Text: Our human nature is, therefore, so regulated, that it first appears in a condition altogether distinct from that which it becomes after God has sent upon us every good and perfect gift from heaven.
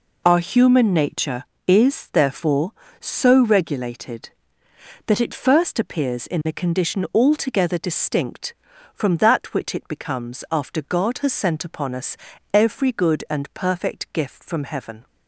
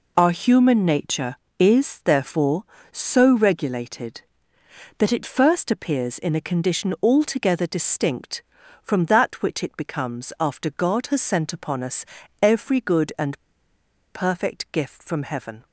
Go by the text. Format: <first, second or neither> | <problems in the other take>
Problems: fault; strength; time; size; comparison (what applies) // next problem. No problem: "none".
first | pauses between "us" and "every"; slight; at 12.0 s; 0.36 s long; slight in the first // pauses between "and" and "perfect"; noticeable; at 13.3 s; 0.78 s long